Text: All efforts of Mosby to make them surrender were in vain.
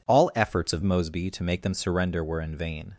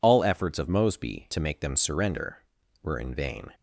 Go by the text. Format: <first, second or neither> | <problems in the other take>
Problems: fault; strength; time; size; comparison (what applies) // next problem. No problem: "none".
second | changes voice at "Mosby"; from 0.8 s on; 2.1 s long